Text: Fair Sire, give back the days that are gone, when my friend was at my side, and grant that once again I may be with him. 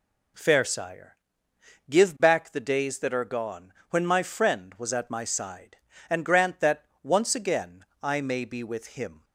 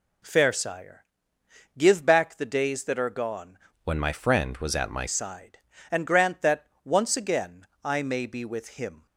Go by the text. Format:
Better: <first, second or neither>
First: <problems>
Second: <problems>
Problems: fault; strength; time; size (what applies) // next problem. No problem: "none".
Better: first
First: pauses between "that" and "once"; slight; at 6.8 s; 0.18 s long // pauses between "again" and "I"; slight; at 7.8 s; 0.18 s long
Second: changes voice from "when" to "my"; from 3.8 to 5.0 s; 1.2 s long // pauses between "that" and "once"; slight; at 6.6 s; 0.18 s long // pauses between "again" and "I"; slight; at 7.6 s; 0.18 s long